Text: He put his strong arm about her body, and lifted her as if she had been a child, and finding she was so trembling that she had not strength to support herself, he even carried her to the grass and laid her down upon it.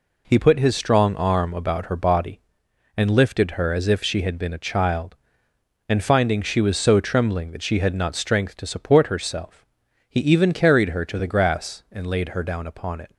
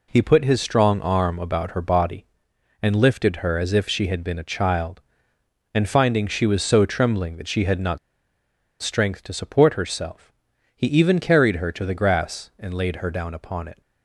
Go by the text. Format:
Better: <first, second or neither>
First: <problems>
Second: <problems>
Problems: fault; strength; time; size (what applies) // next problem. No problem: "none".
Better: first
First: none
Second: pauses between "not" and "strength"; noticeable; at 7.9 s; 0.84 s long